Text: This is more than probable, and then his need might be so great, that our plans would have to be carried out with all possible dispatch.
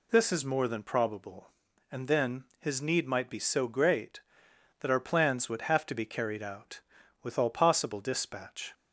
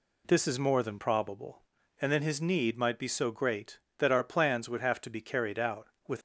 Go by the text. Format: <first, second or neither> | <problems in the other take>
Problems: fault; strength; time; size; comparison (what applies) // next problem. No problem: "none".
first | stops before "all possible dispatch"; at 6.1 s